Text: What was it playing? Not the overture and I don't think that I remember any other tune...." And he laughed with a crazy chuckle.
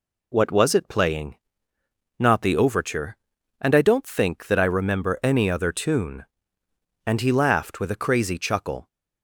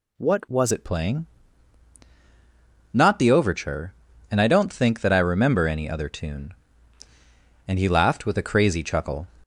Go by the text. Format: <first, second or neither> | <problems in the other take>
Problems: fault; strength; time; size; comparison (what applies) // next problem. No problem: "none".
first | changes voice at "it"; from 0.7 s on; 8.5 s long